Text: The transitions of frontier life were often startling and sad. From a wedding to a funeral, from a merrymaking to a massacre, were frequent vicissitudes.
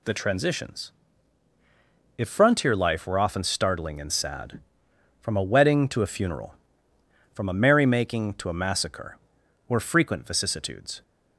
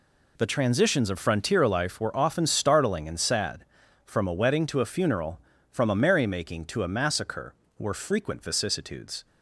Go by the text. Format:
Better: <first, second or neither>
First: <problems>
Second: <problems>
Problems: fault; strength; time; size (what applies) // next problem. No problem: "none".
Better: second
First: says "if" for "of"; at 2.1 s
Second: none